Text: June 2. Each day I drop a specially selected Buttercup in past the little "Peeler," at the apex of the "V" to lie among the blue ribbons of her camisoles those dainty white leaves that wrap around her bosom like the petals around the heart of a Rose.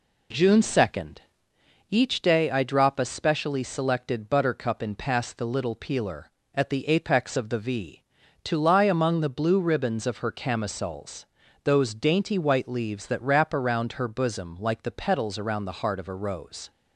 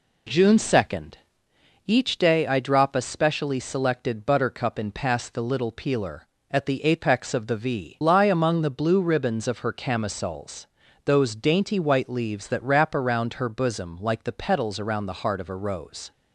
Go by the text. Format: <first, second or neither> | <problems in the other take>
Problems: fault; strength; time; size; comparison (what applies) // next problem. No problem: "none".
first | skips "to"; at 8.0 s // pauses between "camisoles" and "those"; at 10.6 s; 0.38 s long; also in the first